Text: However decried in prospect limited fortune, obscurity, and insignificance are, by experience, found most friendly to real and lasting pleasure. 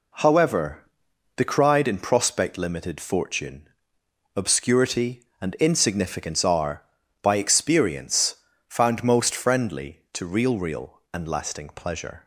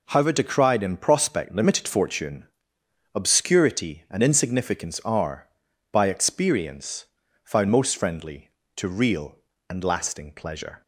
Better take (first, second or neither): second